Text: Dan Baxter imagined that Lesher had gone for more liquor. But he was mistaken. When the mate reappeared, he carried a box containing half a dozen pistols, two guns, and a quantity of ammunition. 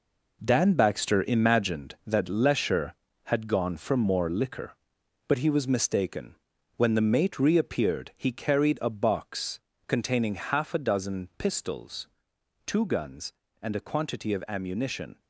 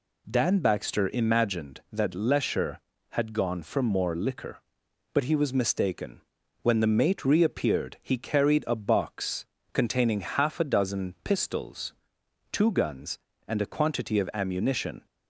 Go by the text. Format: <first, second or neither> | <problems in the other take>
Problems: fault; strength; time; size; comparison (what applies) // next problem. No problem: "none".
second | gets quieter; strong; throughout; 9 dB // pauses between "box" and "containing"; slight; at 9.5 s; 0.26 s long; slight in the second